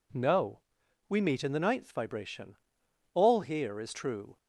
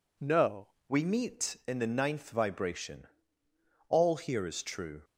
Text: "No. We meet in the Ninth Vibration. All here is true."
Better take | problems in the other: first | changes voice at "We"; from 0.8 s on; 4.2 s long

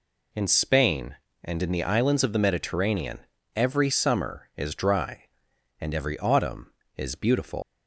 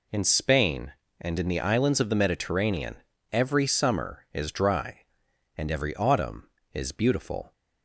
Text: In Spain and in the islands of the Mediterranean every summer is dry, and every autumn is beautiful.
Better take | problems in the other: second | pauses between "Mediterranean" and "every"; slight; at 3.1 s; 0.34 s long; slight in the second // leaves "beautiful" unfinished; at 7.6 s; 135 ms

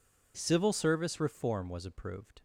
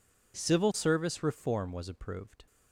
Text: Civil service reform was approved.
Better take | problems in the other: neither | none

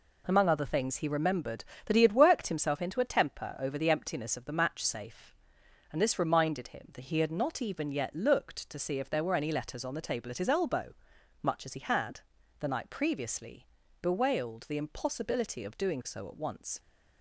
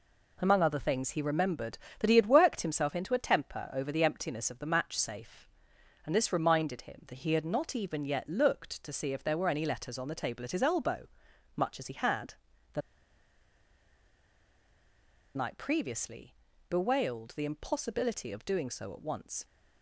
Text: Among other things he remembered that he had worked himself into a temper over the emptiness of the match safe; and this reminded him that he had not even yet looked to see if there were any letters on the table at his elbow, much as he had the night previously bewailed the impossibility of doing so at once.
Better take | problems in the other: first | pauses between "had" and "the"; slight; at 12.3 s; 0.36 s long; slight in the first // pauses between "the" and "night"; strong; at 12.8 s; 2.5 s long // pauses between "previously" and "bewailed"; slight; at 16.3 s; 0.34 s long; slight in the first

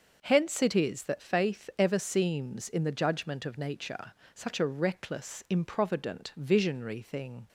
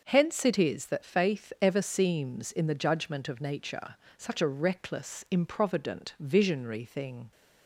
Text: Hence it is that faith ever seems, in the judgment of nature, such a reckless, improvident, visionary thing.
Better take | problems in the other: neither | starts louder than the rest; the same in both

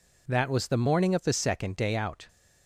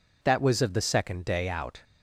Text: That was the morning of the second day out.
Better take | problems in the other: first | skips "the morning"; at 0.6 s

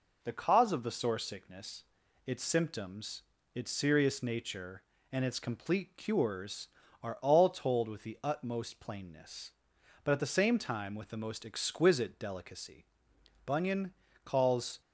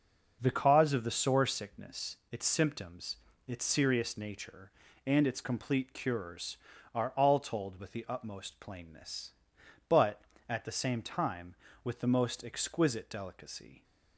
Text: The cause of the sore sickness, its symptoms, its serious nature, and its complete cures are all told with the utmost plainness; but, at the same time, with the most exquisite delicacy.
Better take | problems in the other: second | goes on to say "Bunyan calls"; from 13.4 s on; 1.3 s long

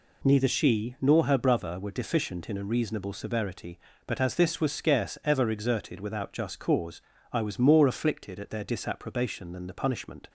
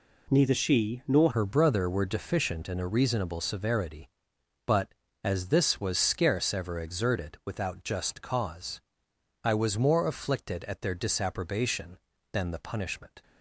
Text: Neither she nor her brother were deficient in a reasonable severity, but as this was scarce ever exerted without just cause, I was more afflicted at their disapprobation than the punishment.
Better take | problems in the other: first | changes voice at "her"; from 1.3 s on; 11.9 s long

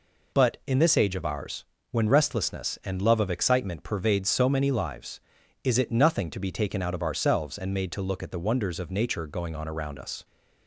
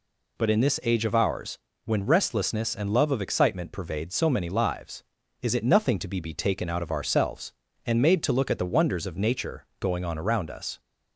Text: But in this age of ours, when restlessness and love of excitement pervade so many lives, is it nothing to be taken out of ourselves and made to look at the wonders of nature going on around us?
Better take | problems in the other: first | says "be" twice; at 6.1 s

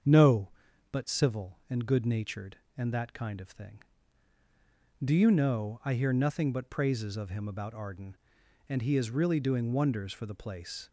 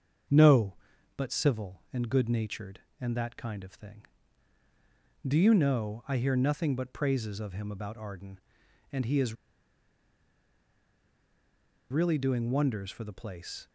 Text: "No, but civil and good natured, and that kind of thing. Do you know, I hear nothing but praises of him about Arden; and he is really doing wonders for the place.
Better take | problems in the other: first | starts louder than the rest; strong; until 1.6 s; 7 dB; strong in the first // pauses between "is" and "really"; strong; at 9.3 s; 2.5 s long

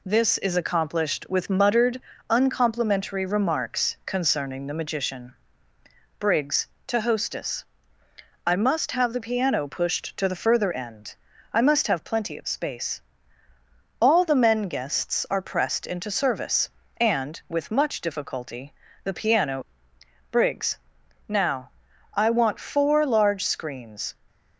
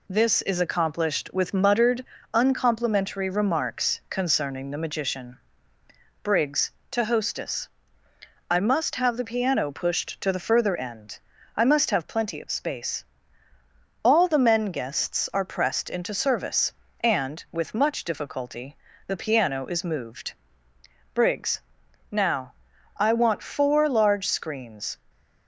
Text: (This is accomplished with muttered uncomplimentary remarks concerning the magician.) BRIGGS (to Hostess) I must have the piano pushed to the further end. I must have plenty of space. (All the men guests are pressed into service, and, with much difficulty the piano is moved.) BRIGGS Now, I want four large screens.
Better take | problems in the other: second | pauses between "muttered" and "uncomplimentary"; slight; at 2.0 s; 0.28 s long; slight in the second // pauses between "difficulty" and "the"; slight; at 18.7 s; 0.30 s long; slight in the second // skips "is moved"; at 19.9 s // pauses between "BRIGGS" and "Now"; noticeable; at 20.7 s; 0.50 s long; noticeable in the second

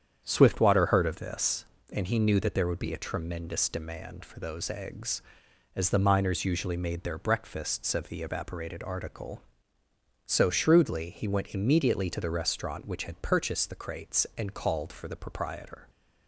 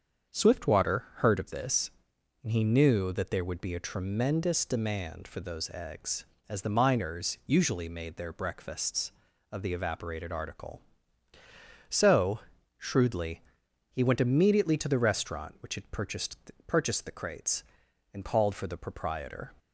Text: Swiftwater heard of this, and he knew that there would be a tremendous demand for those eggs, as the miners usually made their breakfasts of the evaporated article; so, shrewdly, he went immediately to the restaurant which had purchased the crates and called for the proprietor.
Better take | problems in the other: first | starts louder than the rest; strong; until 1.4 s; 7 dB; strong in the first // says "purchased" twice; at 16.6 s

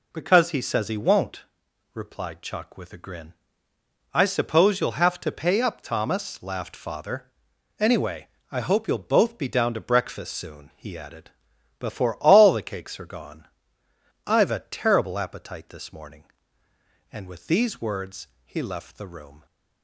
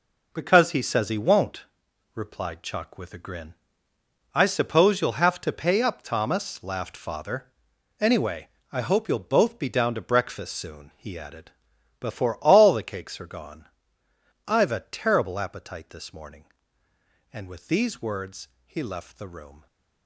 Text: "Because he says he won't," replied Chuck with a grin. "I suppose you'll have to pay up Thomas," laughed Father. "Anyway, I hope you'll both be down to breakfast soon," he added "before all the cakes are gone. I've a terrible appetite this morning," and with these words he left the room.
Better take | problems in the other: first | gets quieter; strong; throughout; 10 dB // pauses between "added" and "before"; noticeable; at 11.4 s; 0.50 s long; noticeable in the first // pauses between "words" and "he"; slight; at 18.4 s; 0.16 s long; slight in the first

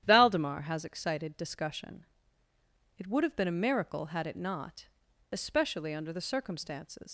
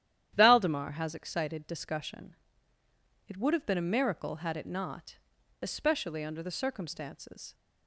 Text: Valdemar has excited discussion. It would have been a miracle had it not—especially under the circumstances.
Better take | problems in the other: second | starts louder than the rest; strong; until 1.0 s; 11 dB; strong in the second // leaves "circumstances" unfinished; at 7.0 s; 105 ms

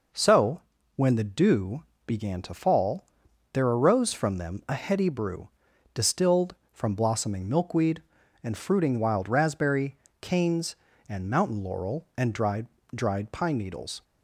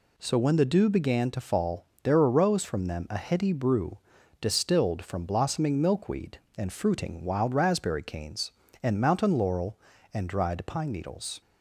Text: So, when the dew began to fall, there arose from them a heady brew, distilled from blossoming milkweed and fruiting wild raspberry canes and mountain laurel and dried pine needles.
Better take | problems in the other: second | pauses between "dew" and "began"; slight; at 1.8 s; 0.22 s long // pauses between "raspberry" and "canes"; slight; at 9.9 s; 0.24 s long // says "dried" twice; at 12.9 s

